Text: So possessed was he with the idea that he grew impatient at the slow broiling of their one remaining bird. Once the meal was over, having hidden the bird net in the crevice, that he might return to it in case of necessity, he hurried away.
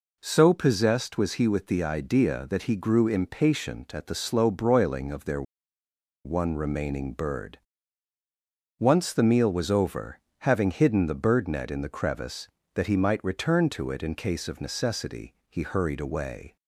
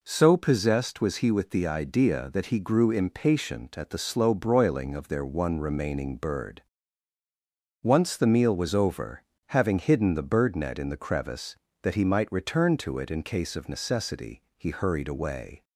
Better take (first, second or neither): second